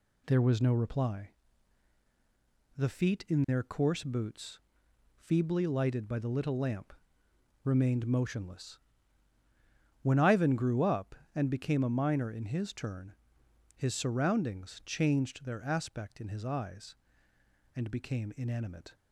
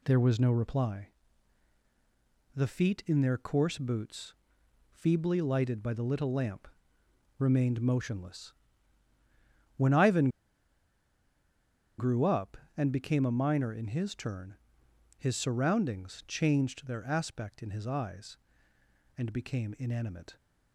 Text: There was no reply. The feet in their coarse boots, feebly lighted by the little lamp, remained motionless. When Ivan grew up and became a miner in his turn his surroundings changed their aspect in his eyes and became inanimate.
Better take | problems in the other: first | pauses between "Ivan" and "grew"; strong; at 10.2 s; 1.7 s long // pauses between "turn" and "his"; noticeable; at 14.5 s; 0.62 s long; noticeable in the first

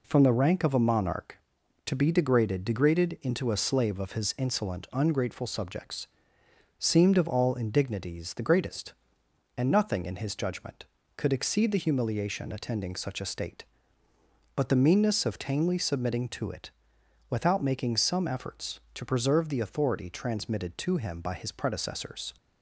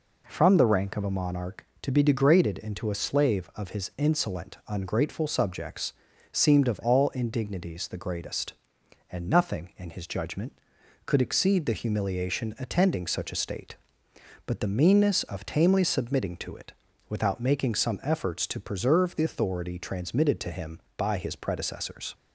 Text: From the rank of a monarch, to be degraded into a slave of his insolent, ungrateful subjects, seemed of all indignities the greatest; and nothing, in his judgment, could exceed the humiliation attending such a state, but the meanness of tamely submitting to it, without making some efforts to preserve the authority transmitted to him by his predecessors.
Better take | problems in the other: second | says "degraded" twice; at 2.6 s

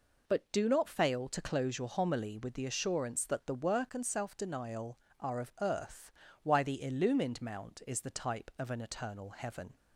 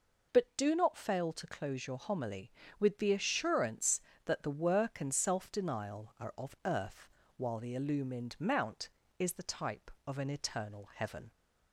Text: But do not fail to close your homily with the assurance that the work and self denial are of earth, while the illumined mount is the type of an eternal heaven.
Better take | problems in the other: second | says "why" for "while"; at 6.4 s

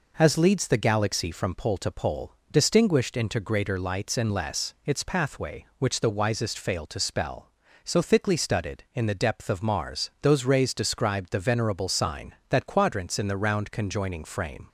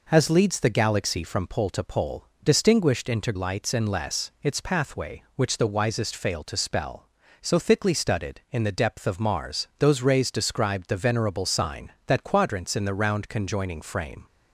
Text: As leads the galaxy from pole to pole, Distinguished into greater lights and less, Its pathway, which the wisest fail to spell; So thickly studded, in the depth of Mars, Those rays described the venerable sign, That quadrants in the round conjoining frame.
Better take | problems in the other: first | skips "greater"; at 3.3 s

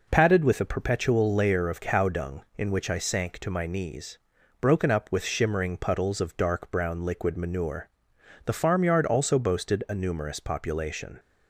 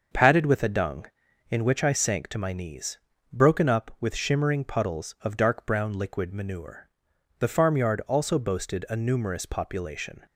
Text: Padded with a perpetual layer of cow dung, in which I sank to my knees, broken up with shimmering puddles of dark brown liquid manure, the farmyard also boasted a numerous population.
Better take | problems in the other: first | starts louder than the rest; until 1.5 s; 6.5 dB // skips "perpetual layer of cow"; at 0.6 s

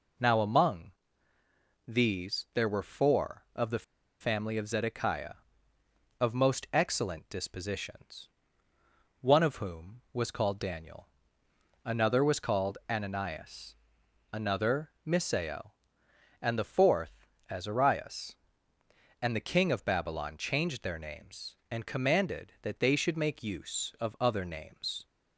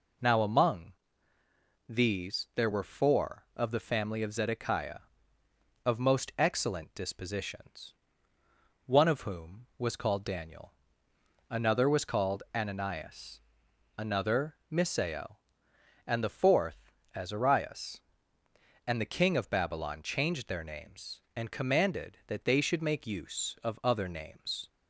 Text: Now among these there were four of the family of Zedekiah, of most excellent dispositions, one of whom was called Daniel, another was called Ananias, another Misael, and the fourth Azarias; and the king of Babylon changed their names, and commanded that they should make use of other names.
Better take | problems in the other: second | pauses between "among" and "these"; noticeable; at 0.9 s; 0.96 s long; noticeable in the second // pauses between "the" and "family"; at 3.8 s; 0.36 s long // pauses between "another" and "Misael"; slight; at 14.9 s; 0.16 s long; slight in the second // pauses between "fourth" and "Azarias"; slight; at 17.2 s; 0.24 s long; slight in the second

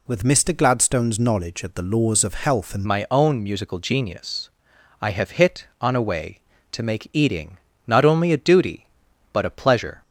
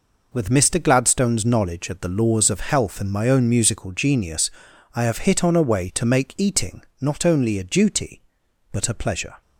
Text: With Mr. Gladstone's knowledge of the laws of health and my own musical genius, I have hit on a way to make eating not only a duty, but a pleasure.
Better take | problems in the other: second | changes voice at "my"; from 2.8 s on; 7.2 s long // pauses between "eating" and "not"; slight; at 7.5 s; 0.30 s long; slight in the second

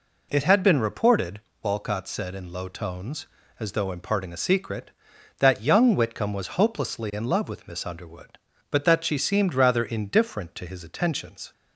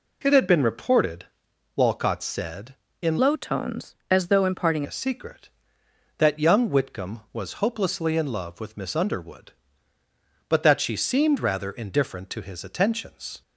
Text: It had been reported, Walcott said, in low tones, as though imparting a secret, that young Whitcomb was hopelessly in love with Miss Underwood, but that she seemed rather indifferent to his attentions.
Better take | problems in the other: first | changes voice from "low" to "imparting"; from 3.1 to 4.8 s; 1.7 s long

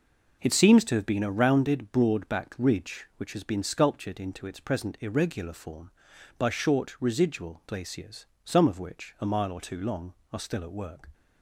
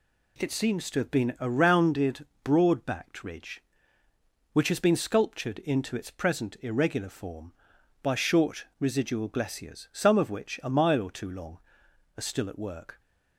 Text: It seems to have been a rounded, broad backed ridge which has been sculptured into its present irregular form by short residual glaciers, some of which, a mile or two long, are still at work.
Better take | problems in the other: neither | none

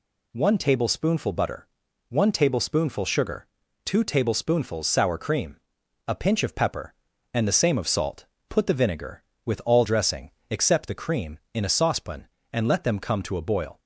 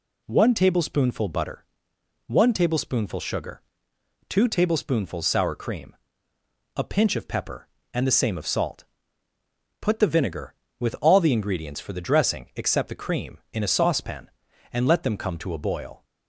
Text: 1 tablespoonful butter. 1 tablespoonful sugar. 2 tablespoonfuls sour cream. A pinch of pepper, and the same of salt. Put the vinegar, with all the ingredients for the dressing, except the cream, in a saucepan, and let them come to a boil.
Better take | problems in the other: second | skips "the ingredients for the"; at 9.8 s

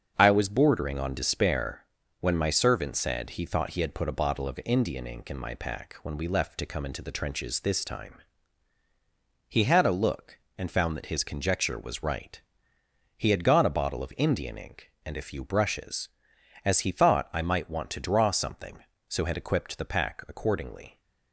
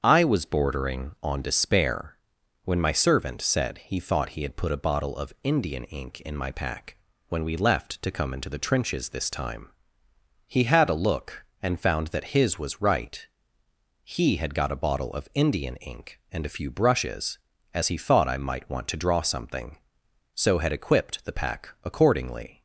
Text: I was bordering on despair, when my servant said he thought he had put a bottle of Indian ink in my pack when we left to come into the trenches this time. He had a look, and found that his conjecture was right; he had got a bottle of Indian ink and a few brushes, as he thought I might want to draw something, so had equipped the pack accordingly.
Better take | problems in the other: first | starts louder than the rest; strong; until 1.0 s; 7.5 dB; also in the first // pauses between "pack" and "when"; slight; at 6.9 s; 0.34 s long // skips "conjecture"; at 12.5 s

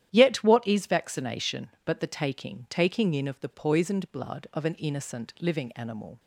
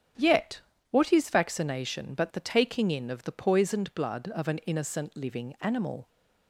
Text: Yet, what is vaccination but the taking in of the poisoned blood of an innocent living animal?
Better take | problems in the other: second | starts louder than the rest; strong; until 1.1 s; 11.5 dB; strong in the second // says "taking" twice; at 2.6 s

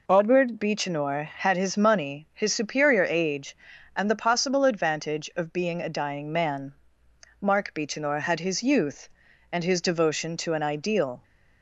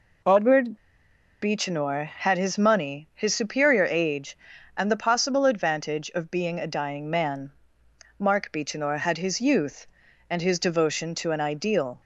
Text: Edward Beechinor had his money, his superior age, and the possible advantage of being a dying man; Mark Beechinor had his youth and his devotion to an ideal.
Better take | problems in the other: first | pauses between "Edward" and "Beechinor"; noticeable; at 0.7 s; 0.65 s long

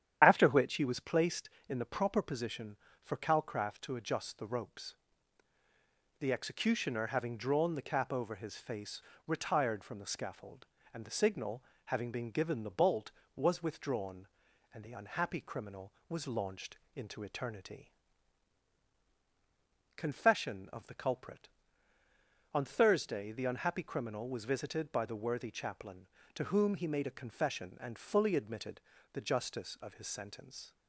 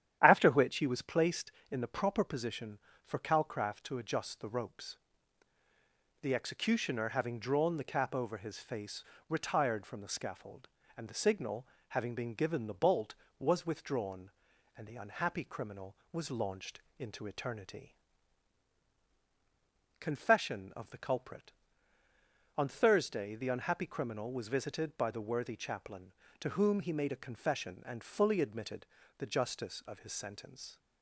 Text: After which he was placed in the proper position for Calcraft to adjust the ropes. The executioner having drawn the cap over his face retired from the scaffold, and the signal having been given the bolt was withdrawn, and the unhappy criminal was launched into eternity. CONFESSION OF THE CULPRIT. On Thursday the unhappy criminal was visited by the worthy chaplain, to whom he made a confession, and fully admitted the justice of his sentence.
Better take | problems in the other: second | loses the start of "After"; at 0.2 s; 30 ms // starts louder than the rest; strong; until 1.2 s; 10 dB; strong in the second // pauses between "face" and "retired"; slight; at 9.0 s; 0.26 s long; slight in the second // pauses between "signal" and "having"; slight; at 11.6 s; 0.22 s long; slight in the second // pauses between "launched" and "into"; slight; at 16.7 s; 0.16 s long; slight in the second // pauses between "admitted" and "the"; slight; at 28.7 s; 0.34 s long; slight in the second

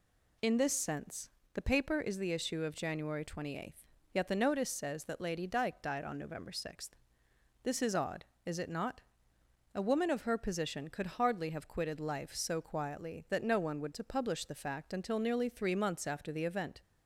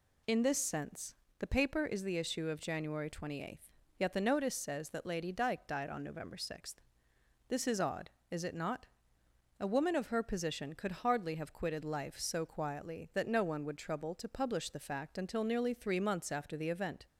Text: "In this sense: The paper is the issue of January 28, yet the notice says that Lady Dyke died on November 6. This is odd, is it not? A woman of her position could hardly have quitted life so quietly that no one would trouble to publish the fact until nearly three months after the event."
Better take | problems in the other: second | skips "trouble"; at 13.9 s

